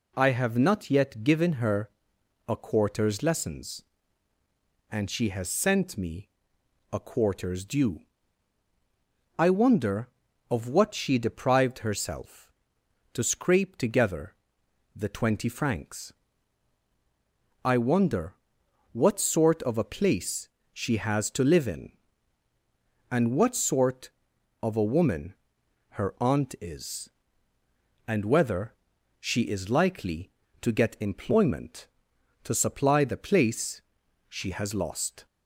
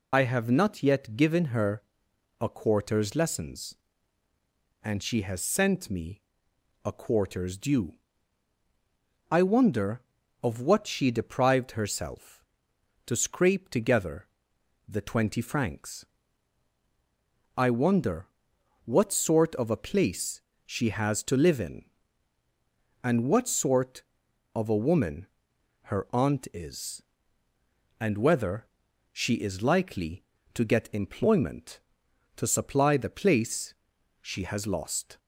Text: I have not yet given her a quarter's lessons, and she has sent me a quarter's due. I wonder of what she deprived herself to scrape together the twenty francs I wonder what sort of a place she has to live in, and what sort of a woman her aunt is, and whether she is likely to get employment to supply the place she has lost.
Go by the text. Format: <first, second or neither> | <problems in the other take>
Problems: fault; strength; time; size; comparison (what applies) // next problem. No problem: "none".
first | loses the start of "I"; at 0.1 s; 50 ms // pauses between "her" and "a"; noticeable; at 1.8 s; 0.56 s long; noticeable in the first // pauses between "me" and "a"; noticeable; at 6.1 s; 0.64 s long; noticeable in the first // pauses between "together" and "the"; noticeable; at 14.2 s; 0.60 s long; noticeable in the first // pauses between "francs" and "I"; strong; at 16.0 s; 1.5 s long; strong in the first // pauses between "wonder" and "what"; noticeable; at 18.2 s; 0.58 s long; noticeable in the first // pauses between "place" and "she"; slight; at 20.4 s; 0.24 s long; slight in the first // pauses between "woman" and "her"; noticeable; at 25.2 s; 0.56 s long; noticeable in the first // pauses between "whether" and "she"; noticeable; at 28.6 s; 0.50 s long; noticeable in the first // pauses between "place" and "she"; noticeable; at 33.7 s; 0.46 s long; noticeable in the first